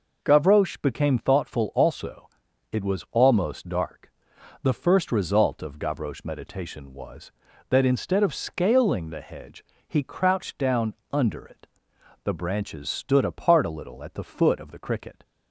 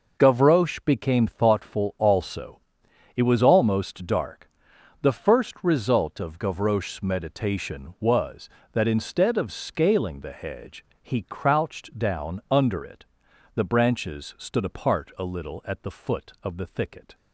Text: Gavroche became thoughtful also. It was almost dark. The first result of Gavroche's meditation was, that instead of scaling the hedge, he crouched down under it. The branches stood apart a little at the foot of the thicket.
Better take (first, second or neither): second